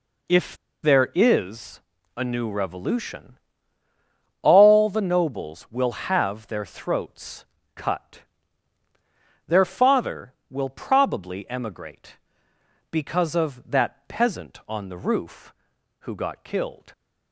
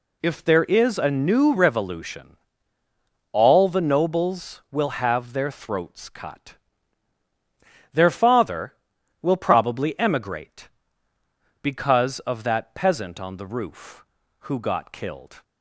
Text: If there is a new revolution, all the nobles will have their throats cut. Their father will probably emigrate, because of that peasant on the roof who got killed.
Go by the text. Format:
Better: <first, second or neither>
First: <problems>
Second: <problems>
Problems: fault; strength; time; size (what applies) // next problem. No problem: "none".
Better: second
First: pauses between "If" and "there"; slight; at 0.5 s; 0.27 s long // pauses between "is" and "a"; slight; at 1.7 s; 0.34 s long // pauses between "throats" and "cut"; slight; at 7.4 s; 0.28 s long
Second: none